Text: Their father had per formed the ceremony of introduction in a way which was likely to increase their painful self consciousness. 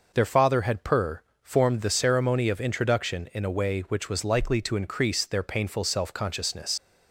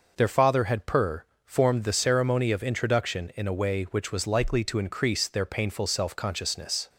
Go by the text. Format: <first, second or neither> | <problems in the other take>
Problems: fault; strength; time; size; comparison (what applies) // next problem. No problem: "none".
second | pauses between "per" and "formed"; slight; at 1.2 s; 0.18 s long; slight in the second // leaves "consciousness" unfinished; at 6.7 s; 85 ms